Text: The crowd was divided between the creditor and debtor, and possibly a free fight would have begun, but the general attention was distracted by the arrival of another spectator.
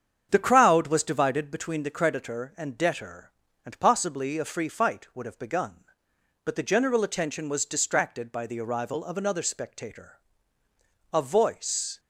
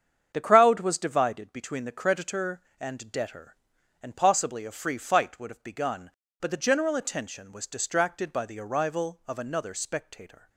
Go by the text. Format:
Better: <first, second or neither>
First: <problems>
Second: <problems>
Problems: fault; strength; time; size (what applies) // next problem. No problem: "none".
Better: second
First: starts louder than the rest; strong; until 1.3 s; 8 dB // goes on to say "A voice"; noticeable; from 11.1 s on; 0.88 s long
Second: starts louder than the rest; strong; until 1.3 s; 8 dB